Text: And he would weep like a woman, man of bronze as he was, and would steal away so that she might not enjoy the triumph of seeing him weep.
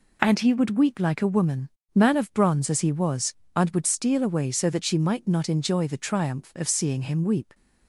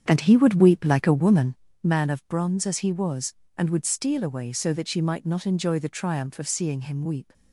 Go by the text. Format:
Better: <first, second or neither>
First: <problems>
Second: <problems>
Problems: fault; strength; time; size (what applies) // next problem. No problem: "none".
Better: first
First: none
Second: starts louder than the rest; strong; until 1.6 s; 8 dB